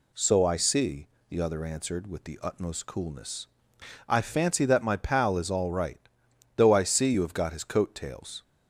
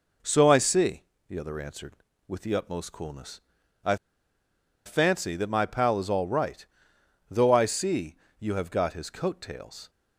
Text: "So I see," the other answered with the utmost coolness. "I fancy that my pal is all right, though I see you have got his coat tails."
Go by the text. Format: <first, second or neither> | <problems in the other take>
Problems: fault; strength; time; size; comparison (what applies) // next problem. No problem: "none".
first | pauses between "I" and "fancy"; noticeable; at 3.9 s; 0.89 s long // pauses between "see" and "you"; slight; at 8.1 s; 0.22 s long